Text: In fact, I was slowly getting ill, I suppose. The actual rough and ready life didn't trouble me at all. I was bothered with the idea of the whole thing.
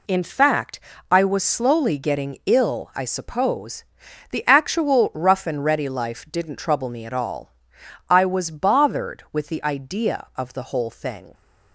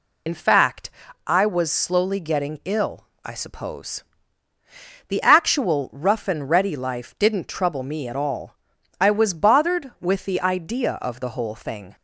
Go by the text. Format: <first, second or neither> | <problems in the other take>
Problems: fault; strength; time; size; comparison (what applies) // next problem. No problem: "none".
first | loses the start of "In"; at 0.2 s; 50 ms